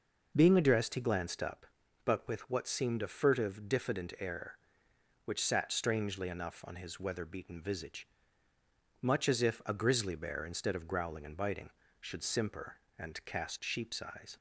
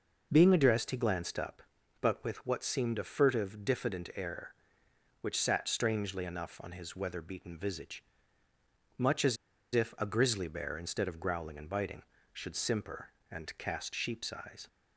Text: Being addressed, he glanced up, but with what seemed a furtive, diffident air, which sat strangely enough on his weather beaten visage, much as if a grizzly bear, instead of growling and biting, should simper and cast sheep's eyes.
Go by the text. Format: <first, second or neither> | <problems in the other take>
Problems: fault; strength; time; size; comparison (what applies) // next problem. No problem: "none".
first | pauses between "as" and "if"; at 9.3 s; 0.38 s long